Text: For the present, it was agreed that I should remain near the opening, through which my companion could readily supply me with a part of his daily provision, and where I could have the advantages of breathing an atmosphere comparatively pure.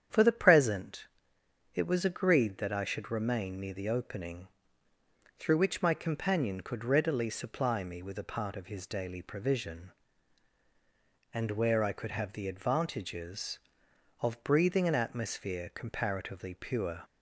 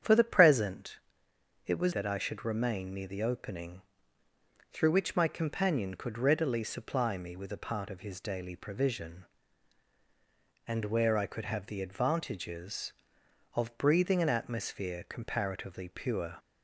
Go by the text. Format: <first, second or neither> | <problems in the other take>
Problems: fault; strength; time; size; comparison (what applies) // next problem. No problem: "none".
first | starts louder than the rest; strong; until 1.6 s; 8.5 dB; strong in the first // skips "agreed"; at 1.9 s